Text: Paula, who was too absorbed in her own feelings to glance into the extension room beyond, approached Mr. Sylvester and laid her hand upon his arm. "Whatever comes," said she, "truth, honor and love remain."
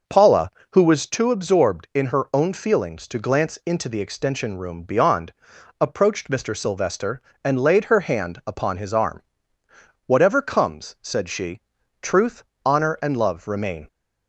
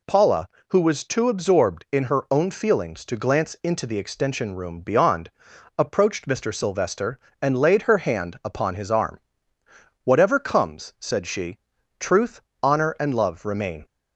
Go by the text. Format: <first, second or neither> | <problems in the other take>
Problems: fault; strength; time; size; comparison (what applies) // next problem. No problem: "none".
second | starts louder than the rest; noticeable; until 1.2 s; 6 dB